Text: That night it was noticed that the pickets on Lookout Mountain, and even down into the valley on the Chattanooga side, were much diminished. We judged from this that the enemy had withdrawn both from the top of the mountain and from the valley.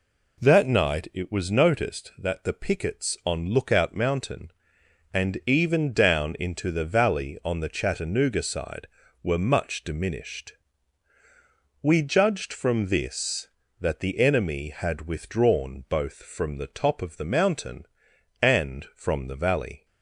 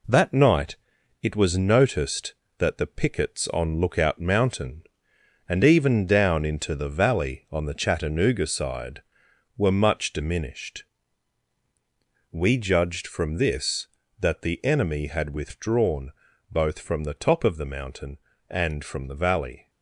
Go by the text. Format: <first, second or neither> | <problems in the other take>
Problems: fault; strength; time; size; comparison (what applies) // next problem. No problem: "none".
first | gets quieter; noticeable; throughout; 5.5 dB // pauses between "night" and "it"; noticeable; at 0.7 s; 0.46 s long // pauses between "withdrawn" and "both"; at 16.1 s; 0.40 s long